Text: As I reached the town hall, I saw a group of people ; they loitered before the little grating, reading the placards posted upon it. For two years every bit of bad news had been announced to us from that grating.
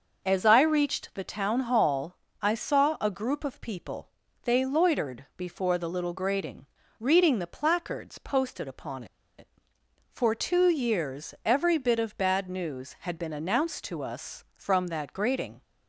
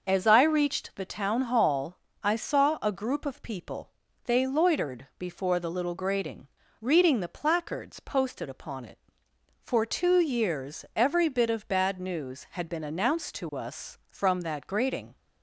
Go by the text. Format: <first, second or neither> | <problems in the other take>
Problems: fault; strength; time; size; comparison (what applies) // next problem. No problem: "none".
second | starts louder than the rest; noticeable; until 1.2 s; 6 dB; also in the second // pauses between "upon" and "it"; slight; at 9.0 s; 0.33 s long